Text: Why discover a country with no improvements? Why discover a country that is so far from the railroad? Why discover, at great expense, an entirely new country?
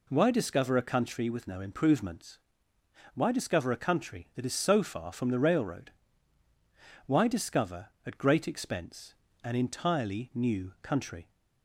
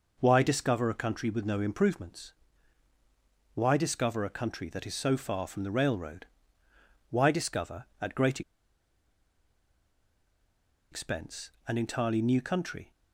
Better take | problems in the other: first | pauses between "great" and "expense"; strong; at 8.4 s; 2.5 s long

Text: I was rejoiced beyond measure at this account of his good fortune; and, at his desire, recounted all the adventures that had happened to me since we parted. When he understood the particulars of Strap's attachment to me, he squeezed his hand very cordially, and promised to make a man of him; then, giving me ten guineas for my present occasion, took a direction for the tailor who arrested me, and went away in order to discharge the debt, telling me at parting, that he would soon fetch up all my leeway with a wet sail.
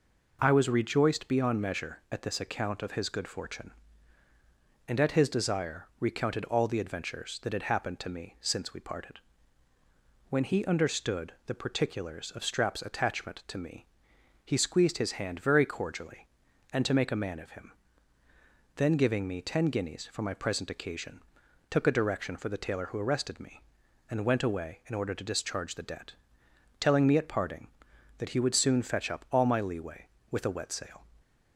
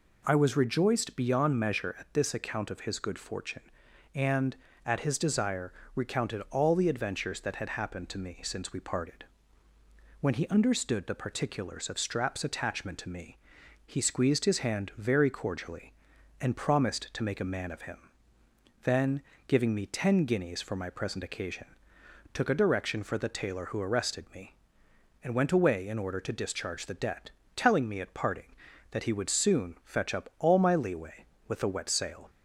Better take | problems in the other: second | skips "promised"; at 16.8 s

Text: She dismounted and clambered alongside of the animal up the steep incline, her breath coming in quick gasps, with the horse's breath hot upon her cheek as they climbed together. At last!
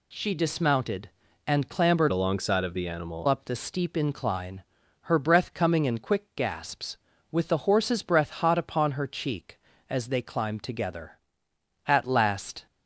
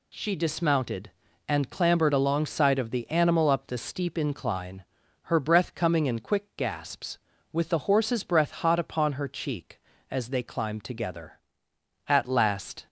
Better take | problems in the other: second | changes voice from "alongside" to "animal"; from 2.1 to 3.2 s; 1.1 s long

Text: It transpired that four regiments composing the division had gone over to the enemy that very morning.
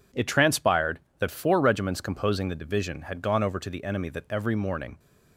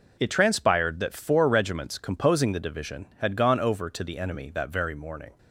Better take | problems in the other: second | says "every" for "very"; at 4.2 s

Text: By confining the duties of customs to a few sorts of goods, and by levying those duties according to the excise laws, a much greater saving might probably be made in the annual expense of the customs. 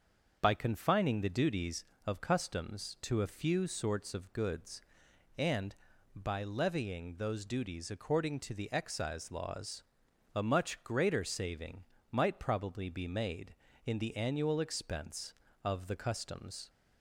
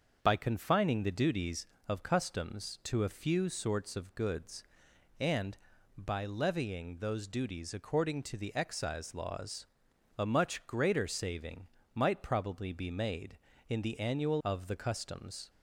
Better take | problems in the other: first | starts louder than the rest; until 1.2 s; 6.5 dB; also in the first // pauses between "saving" and "might"; slight; at 11.6 s; 0.28 s long; slight in the first // skips "expense"; at 14.4 s

